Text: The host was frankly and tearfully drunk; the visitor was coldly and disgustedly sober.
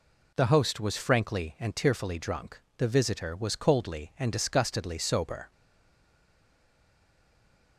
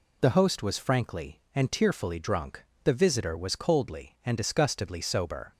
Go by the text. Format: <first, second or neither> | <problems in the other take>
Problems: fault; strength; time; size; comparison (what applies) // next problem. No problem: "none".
second | stays silent after the last word; from 5.5 s on; 2.2 s long